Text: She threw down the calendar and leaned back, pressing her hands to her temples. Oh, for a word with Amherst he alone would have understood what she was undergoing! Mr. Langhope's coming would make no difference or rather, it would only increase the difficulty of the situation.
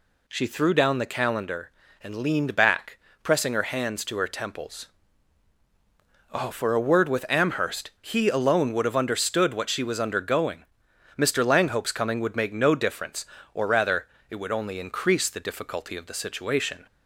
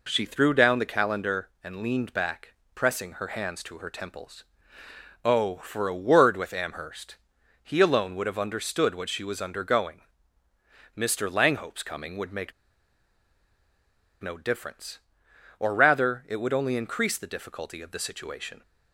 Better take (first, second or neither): first